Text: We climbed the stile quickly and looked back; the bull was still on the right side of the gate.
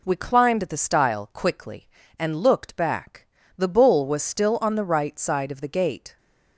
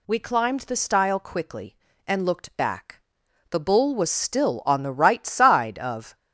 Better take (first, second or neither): first